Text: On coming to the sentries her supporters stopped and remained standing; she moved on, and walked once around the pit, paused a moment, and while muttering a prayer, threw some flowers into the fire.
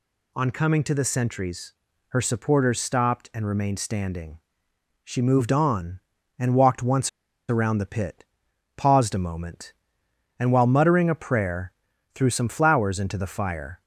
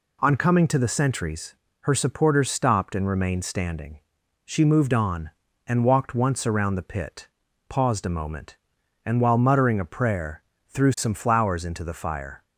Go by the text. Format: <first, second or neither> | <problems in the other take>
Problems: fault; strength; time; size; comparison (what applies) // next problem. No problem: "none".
second | pauses between "sentries" and "her"; slight; at 1.7 s; 0.34 s long; slight in the second // pauses between "once" and "around"; at 7.0 s; 0.40 s long